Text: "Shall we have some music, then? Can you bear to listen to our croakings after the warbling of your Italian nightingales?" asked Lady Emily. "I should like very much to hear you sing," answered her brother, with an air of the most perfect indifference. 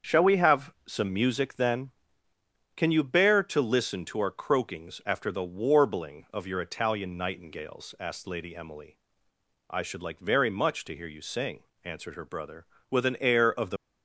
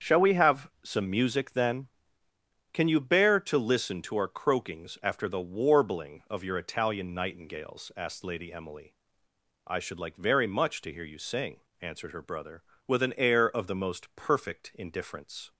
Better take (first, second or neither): second